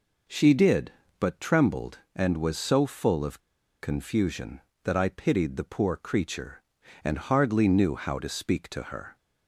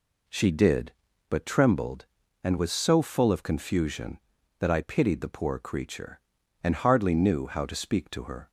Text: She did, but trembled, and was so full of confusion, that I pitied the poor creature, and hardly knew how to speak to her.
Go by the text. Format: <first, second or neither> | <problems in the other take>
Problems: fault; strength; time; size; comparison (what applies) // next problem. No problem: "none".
second | pauses between "of" and "confusion"; at 3.4 s; 0.40 s long